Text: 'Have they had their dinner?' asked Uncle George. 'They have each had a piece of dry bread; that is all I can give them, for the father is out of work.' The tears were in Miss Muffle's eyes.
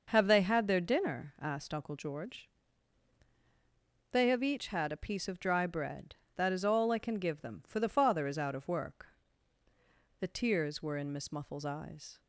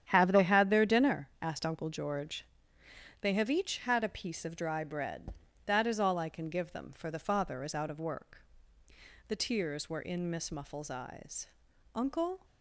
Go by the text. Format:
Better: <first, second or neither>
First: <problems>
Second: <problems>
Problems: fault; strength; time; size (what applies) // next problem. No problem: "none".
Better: first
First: none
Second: starts louder than the rest; strong; until 1.0 s; 9.5 dB // goes on to say "Uncle"; from 11.9 s on; 0.50 s long